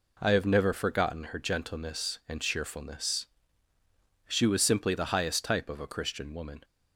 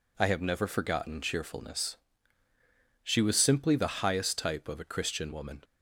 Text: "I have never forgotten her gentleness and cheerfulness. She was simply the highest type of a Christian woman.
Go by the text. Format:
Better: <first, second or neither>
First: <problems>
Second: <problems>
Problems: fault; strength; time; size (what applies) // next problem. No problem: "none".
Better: first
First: none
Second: skips "her gentleness and"; at 1.2 s